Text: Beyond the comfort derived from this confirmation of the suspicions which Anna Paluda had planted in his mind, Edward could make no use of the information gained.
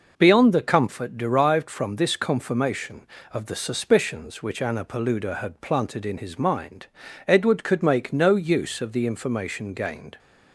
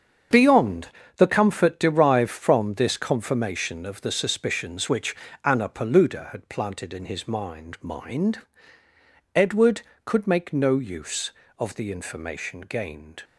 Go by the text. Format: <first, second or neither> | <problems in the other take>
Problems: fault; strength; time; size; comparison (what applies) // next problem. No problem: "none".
first | starts louder than the rest; strong; until 1.6 s; 7 dB // pauses between "Beyond" and "the"; slight; at 0.8 s; 0.30 s long // pauses between "which" and "Anna"; slight; at 5.1 s; 0.30 s long // says "mind" twice; at 7.8 s